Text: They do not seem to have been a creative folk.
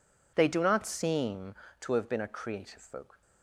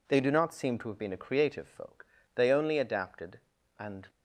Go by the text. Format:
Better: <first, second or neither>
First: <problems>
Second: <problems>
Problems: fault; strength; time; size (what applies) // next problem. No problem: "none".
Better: first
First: none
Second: goes on to say "They only adapted and"; strong; from 2.3 s on; 1.7 s long